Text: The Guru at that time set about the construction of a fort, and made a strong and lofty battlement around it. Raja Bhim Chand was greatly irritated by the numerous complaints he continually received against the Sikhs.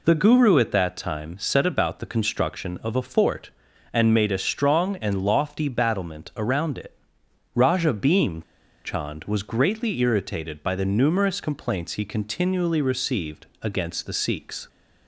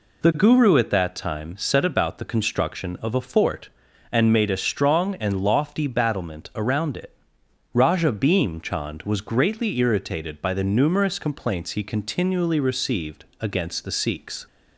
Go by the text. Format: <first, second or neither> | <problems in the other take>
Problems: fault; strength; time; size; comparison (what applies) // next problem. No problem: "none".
second | pauses between "Bhim" and "Chand"; at 8.4 s; 0.41 s long